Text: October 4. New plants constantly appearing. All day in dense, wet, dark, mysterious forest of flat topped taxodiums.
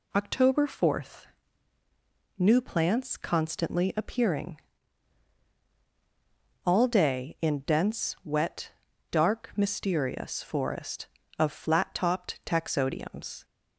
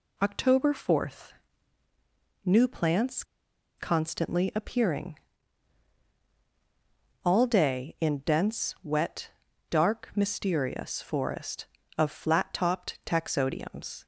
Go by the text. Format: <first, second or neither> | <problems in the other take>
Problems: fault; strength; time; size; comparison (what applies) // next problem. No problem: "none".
first | pauses between "plants" and "constantly"; noticeable; at 3.2 s; 0.54 s long